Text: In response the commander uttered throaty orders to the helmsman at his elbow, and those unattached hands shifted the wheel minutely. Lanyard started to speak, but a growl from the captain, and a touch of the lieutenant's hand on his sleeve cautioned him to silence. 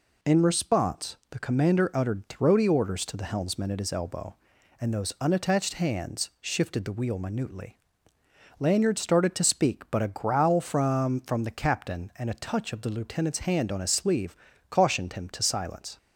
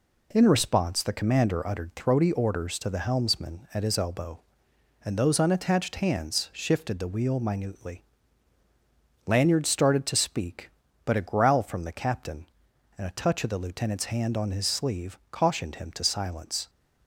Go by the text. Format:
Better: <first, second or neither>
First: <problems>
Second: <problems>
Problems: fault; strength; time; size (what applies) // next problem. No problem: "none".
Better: second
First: says "from" twice; at 11.2 s // pauses between "sleeve" and "cautioned"; slight; at 14.3 s; 0.34 s long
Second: none